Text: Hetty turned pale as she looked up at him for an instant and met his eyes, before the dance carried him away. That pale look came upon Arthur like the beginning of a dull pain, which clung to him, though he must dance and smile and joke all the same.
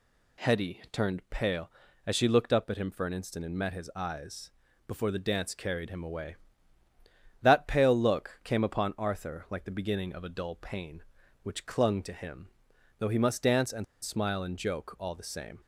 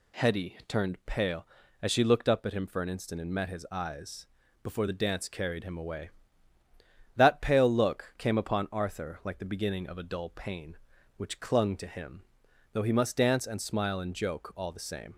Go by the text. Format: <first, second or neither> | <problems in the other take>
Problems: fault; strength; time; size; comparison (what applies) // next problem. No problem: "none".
second | pauses between "and" and "smile"; slight; at 13.8 s; 0.17 s long